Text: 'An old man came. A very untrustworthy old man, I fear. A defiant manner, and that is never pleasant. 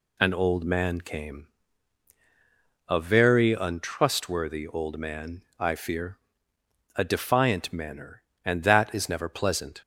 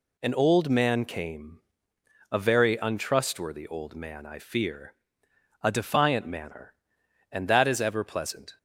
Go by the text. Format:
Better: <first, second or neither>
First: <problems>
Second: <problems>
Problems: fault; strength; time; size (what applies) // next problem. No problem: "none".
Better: first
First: none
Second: says "ever" for "never"; at 7.7 s